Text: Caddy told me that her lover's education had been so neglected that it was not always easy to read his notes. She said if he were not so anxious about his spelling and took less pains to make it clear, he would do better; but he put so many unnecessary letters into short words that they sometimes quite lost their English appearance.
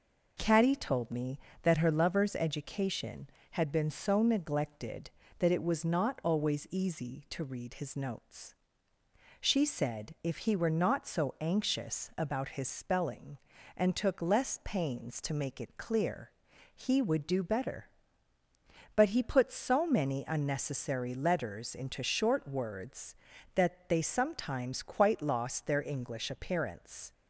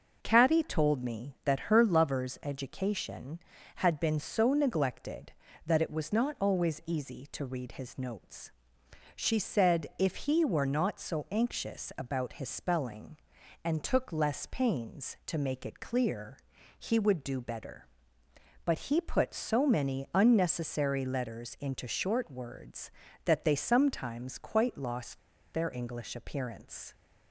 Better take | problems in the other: first | pauses between "lost" and "their"; slight; at 25.1 s; 0.35 s long

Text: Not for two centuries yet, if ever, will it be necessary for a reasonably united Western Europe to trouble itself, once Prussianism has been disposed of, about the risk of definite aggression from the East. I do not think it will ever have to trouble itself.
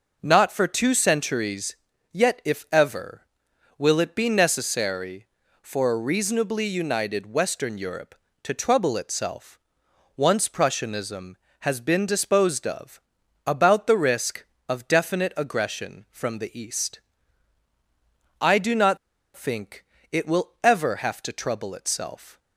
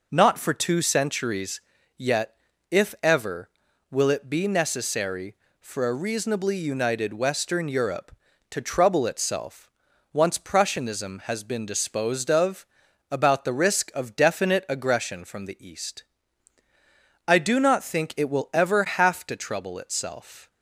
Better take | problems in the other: second | pauses between "centuries" and "yet"; slight; at 1.7 s; 0.36 s long; slight in the second // pauses between "not" and "think"; at 18.9 s; 0.38 s long // pauses between "think" and "it"; slight; at 19.8 s; 0.26 s long

